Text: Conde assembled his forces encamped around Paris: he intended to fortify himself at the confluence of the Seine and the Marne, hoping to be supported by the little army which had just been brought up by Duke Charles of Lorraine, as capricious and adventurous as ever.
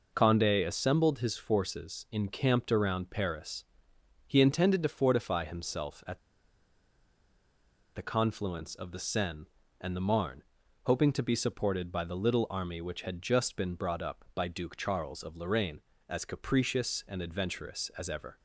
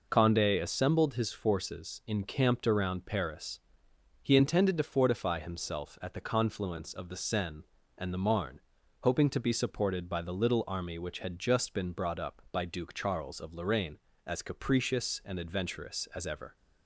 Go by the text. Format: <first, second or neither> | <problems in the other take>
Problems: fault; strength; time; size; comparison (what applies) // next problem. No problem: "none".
second | pauses between "at" and "the"; strong; at 6.1 s; 1.7 s long